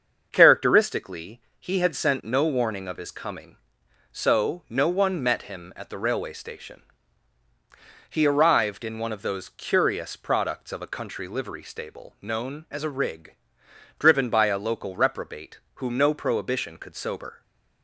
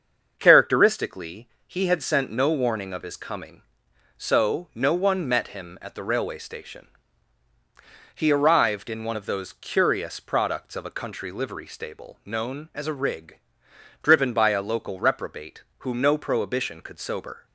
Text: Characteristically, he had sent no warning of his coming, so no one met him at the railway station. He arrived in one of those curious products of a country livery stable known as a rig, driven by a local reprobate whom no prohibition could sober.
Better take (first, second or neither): neither